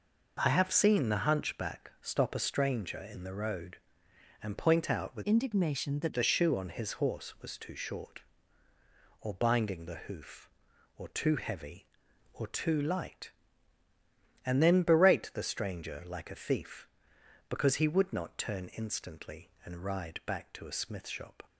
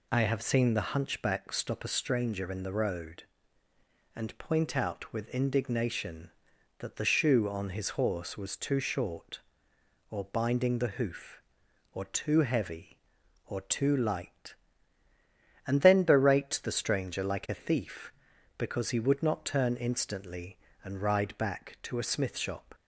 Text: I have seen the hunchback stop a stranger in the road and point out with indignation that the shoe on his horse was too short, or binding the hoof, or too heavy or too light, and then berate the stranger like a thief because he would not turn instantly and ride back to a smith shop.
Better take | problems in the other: second | changes voice from "indignation" to "that"; from 5.2 to 6.1 s; 0.9 s long

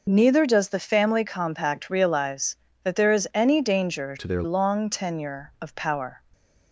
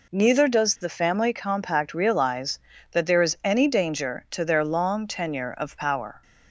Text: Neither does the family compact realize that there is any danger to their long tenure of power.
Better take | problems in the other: second | changes voice from "to" to "their"; from 4.1 to 4.4 s; 0.3 s long

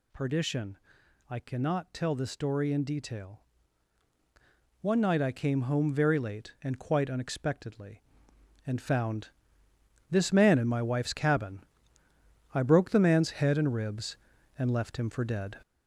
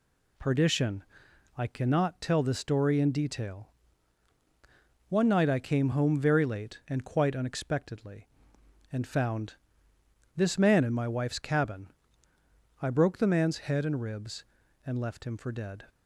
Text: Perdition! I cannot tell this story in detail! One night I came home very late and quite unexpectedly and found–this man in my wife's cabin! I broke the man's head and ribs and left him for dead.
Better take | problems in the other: second | gets louder; noticeable; throughout; 6 dB

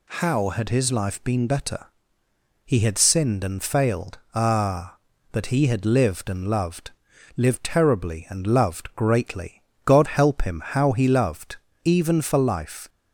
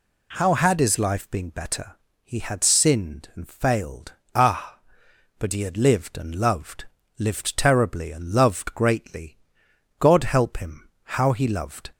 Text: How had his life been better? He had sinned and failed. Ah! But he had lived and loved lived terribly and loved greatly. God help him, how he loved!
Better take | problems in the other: second | pauses between "loved" and "lived"; noticeable; at 6.9 s; 0.46 s long; slight in the second // goes on to say "Even for life"; noticeable; from 11.8 s on; 1.0 s long

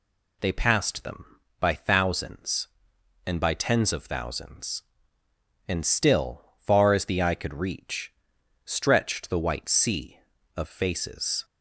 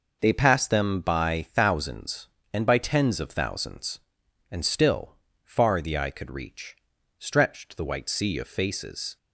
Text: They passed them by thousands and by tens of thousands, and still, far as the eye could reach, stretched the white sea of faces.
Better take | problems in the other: first | skips "as"; at 5.8 s

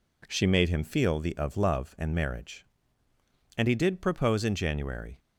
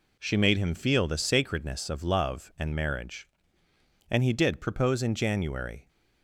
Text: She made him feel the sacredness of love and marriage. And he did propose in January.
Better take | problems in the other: second | skips "sacredness"; at 1.3 s

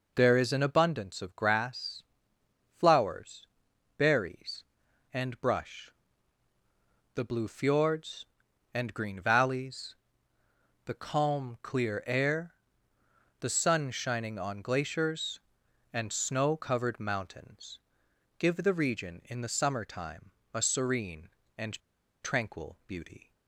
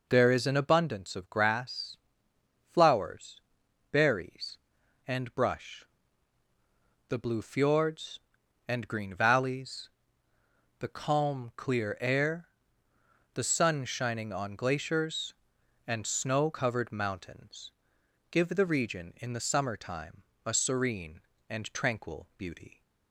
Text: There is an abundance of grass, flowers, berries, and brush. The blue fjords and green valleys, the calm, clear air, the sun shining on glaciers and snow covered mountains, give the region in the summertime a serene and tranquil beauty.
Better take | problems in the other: second | pauses between "summertime" and "a"; slight; at 20.3 s; 0.22 s long; slight in the second // pauses between "and" and "tranquil"; at 21.8 s; 0.41 s long

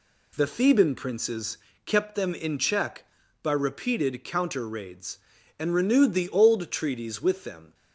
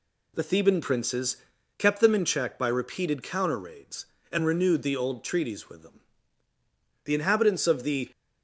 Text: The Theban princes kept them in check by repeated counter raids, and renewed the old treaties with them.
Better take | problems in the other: first | pauses between "princes" and "kept"; at 1.3 s; 0.42 s long; slight in the first // goes on to say "The inhabitants of the"; noticeable; from 7.0 s on; 1.0 s long

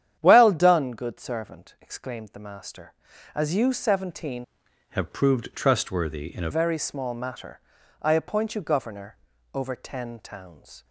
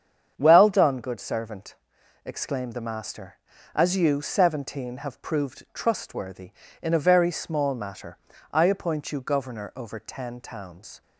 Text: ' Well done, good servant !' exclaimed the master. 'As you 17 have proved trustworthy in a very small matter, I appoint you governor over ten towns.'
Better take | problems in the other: second | starts louder than the rest; strong; until 1.1 s; 10 dB; strong in the second // changes voice from "have" to "a"; from 4.8 to 6.4 s; 1.6 s long // pauses between "governor" and "over"; at 9.1 s; 0.38 s long

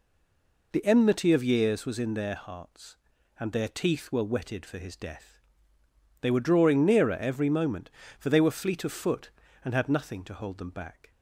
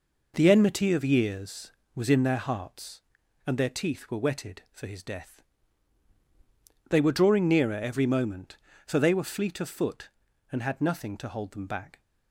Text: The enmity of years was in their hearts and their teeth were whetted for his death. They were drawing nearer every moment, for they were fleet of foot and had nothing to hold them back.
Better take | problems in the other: second | stays silent before the first word; slight; until 0.7 s; 0.7 s long

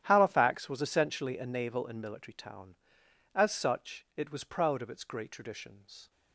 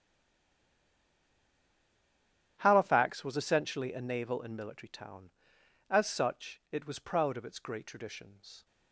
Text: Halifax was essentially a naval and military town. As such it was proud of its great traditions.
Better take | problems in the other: first | stays silent before the first word; strong; until 2.5 s; 2.5 s long // starts louder than the rest; strong; until 3.6 s; 11 dB; strong in the first

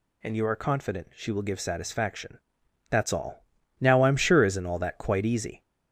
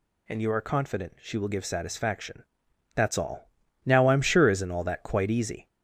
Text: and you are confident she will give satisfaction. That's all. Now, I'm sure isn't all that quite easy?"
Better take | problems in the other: neither | none

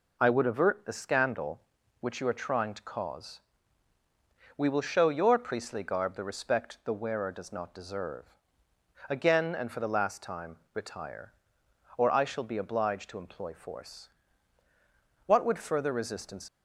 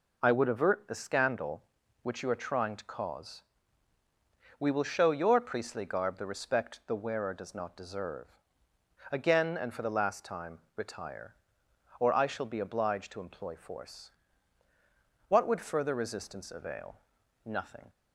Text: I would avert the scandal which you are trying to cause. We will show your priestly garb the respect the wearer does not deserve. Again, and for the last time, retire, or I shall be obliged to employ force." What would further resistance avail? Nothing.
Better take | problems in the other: second | stops before "avail Nothing"; at 16.4 s

